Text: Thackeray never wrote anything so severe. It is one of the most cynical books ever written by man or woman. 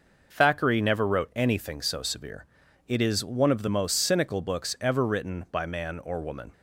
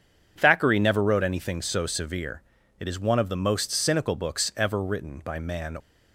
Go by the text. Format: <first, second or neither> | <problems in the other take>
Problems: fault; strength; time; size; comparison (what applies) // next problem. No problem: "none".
first | stops before "or woman"; at 5.7 s